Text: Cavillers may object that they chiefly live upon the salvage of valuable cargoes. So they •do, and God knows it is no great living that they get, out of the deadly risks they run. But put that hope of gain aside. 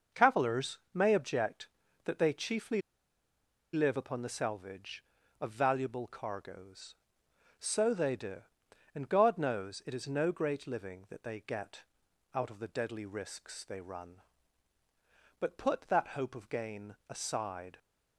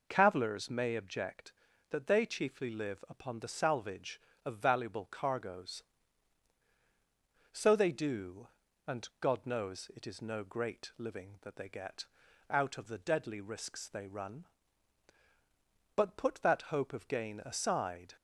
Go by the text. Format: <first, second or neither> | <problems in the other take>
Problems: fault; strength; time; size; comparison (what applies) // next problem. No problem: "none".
second | starts louder than the rest; until 1.2 s; 6 dB // pauses between "chiefly" and "live"; noticeable; at 2.8 s; 0.92 s long